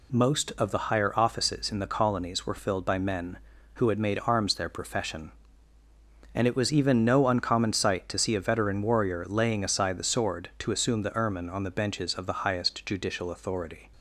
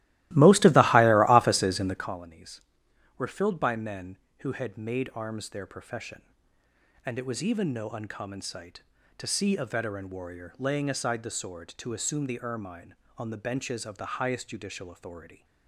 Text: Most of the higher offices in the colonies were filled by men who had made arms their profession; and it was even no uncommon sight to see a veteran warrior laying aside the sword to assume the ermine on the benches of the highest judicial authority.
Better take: first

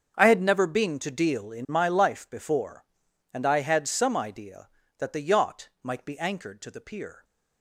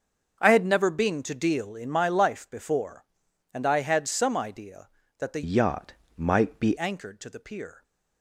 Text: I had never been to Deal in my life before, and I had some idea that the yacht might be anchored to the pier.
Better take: first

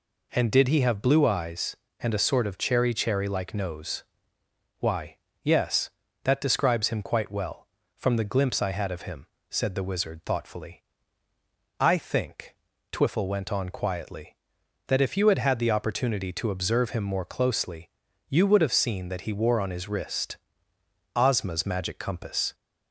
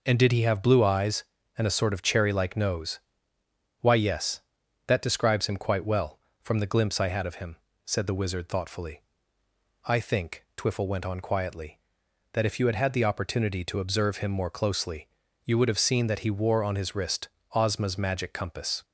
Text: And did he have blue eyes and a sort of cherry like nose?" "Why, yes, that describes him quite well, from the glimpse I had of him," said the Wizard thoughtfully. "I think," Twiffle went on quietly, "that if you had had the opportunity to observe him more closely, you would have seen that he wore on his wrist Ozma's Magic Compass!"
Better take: second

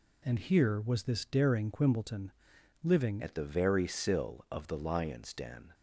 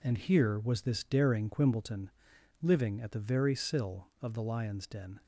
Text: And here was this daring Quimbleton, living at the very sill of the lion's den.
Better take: second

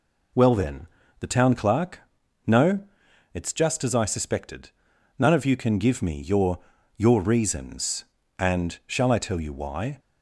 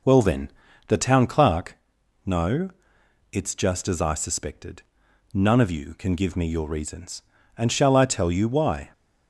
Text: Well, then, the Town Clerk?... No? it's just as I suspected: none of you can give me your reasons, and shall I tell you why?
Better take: second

